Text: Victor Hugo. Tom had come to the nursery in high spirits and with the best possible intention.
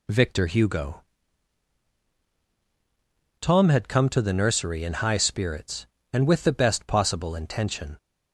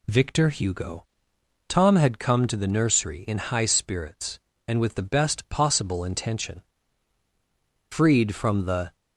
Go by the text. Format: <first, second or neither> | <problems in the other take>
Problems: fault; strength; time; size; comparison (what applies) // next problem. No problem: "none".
first | goes on to say "Freed from the"; noticeable; from 7.8 s on; 1.0 s long